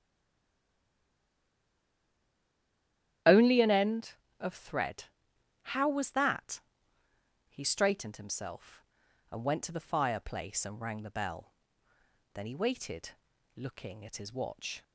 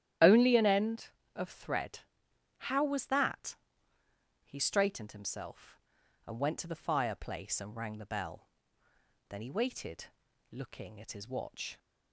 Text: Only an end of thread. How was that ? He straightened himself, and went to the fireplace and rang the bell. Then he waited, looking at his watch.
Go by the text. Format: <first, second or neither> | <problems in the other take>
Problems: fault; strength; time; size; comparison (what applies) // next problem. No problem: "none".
second | stays silent before the first word; strong; until 3.2 s; 3.2 s long // starts louder than the rest; strong; until 4.5 s; 11.5 dB; strong in the second